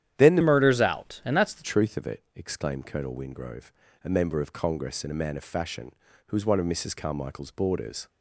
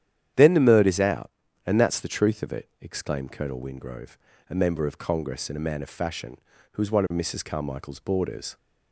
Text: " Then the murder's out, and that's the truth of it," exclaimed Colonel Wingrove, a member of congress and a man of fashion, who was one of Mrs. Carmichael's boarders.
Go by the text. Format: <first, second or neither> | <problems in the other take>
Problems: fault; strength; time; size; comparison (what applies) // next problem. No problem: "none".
second | starts louder than the rest; strong; until 1.1 s; 10.5 dB; strong in the second // changes voice from "murder's" to "the"; from 0.4 to 1.6 s; 1.2 s long